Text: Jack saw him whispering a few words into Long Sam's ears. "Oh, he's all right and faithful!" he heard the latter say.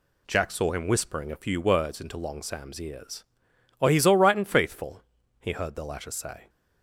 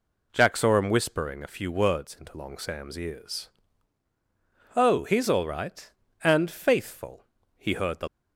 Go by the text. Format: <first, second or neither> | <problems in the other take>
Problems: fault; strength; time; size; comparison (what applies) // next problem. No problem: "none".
first | stops before "latter say"; at 8.0 s